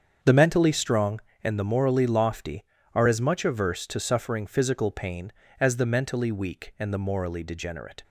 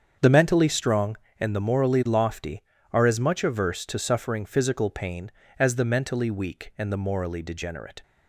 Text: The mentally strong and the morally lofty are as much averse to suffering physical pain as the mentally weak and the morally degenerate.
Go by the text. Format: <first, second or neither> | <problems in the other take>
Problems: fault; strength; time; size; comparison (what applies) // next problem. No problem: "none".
neither | starts louder than the rest; strong; the same in both